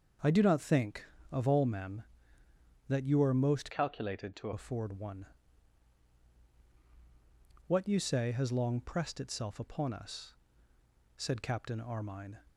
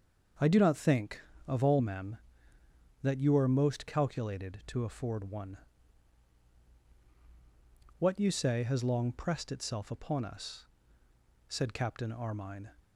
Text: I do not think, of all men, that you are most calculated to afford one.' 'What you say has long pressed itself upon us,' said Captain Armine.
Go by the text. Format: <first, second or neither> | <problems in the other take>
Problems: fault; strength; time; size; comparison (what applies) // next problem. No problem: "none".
second | starts louder than the rest; until 1.4 s; 6.5 dB; also in the second // changes voice from "calculated" to "to"; from 3.7 to 4.5 s; 0.8 s long